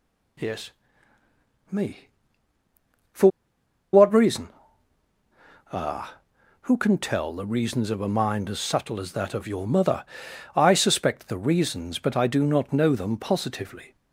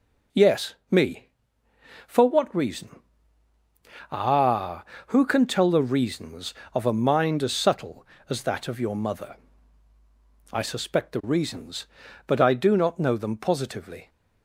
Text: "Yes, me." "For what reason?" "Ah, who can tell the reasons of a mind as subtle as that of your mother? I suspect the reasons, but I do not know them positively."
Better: second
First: pauses between "For" and "what"; noticeable; at 3.2 s; 0.64 s long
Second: none

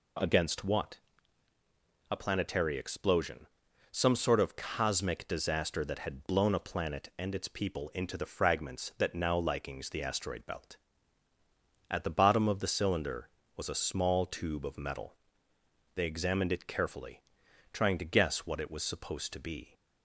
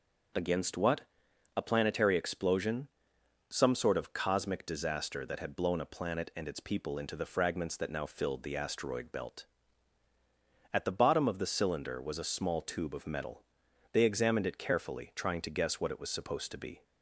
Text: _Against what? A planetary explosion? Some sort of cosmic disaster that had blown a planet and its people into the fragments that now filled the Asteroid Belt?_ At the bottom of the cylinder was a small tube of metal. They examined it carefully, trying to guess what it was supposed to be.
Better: second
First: says "likings" for "filled"; at 9.3 s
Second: none

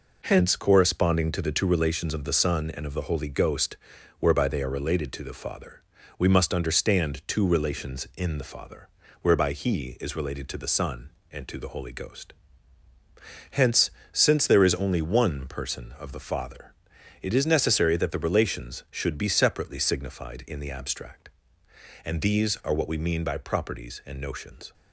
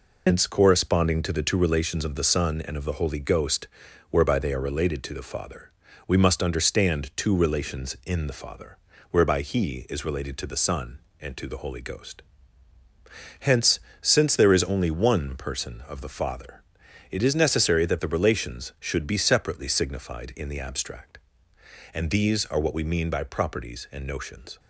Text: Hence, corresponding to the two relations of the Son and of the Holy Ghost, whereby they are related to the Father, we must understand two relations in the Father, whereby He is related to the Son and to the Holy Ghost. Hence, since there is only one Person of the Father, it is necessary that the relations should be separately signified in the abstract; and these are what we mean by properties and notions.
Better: first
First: none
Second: loses the start of "Hence"; at 0.2 s; 120 ms

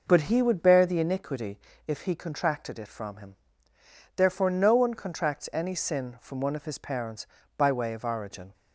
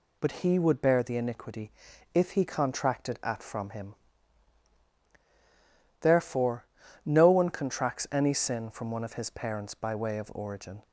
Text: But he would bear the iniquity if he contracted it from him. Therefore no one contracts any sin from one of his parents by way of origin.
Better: first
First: pauses between "iniquity" and "if"; slight; at 1.5 s; 0.26 s long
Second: pauses between "iniquity" and "if"; at 1.7 s; 0.42 s long // says "at" for "it"; at 3.2 s // pauses between "Therefore" and "no"; at 6.6 s; 0.40 s long

